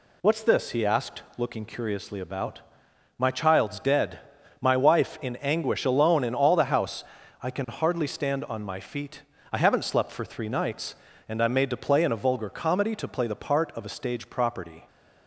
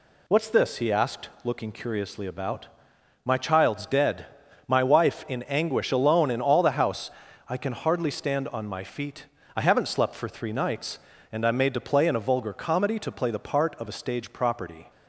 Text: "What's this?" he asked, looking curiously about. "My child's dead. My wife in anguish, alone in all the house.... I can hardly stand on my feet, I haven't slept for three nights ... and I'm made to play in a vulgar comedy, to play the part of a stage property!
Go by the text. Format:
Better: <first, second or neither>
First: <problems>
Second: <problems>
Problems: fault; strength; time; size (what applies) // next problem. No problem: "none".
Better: neither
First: none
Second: none